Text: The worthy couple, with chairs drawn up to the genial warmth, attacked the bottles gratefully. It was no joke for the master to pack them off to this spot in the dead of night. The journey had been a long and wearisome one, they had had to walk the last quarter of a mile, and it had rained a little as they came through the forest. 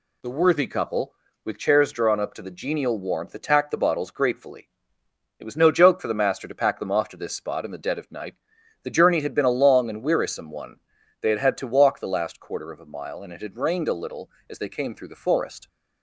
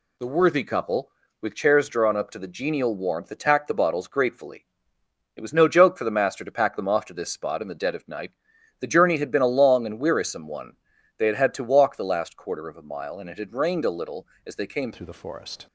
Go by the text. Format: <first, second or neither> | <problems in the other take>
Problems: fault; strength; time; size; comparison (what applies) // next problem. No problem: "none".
first | changes voice at "through"; from 14.9 s on; 0.7 s long